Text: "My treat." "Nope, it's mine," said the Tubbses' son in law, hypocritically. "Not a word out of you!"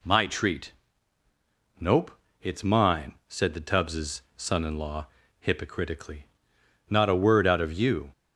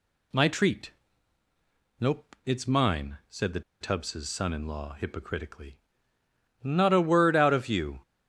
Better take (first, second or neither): first